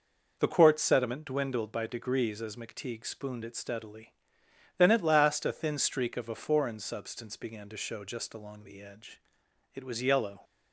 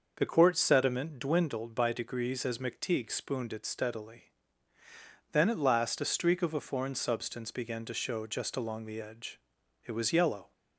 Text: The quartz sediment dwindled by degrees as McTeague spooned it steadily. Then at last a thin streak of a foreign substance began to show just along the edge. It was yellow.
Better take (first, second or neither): first